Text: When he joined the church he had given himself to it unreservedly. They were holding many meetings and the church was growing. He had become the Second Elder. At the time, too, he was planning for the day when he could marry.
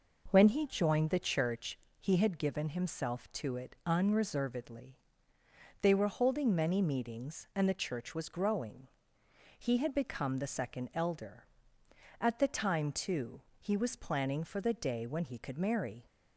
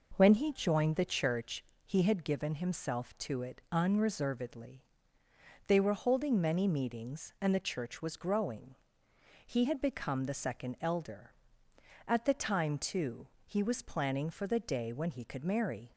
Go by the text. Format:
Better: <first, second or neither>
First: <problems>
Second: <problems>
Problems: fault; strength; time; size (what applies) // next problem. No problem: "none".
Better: neither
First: pauses between "church" and "he"; slight; at 1.7 s; 0.22 s long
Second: pauses between "church" and "he"; slight; at 1.6 s; 0.22 s long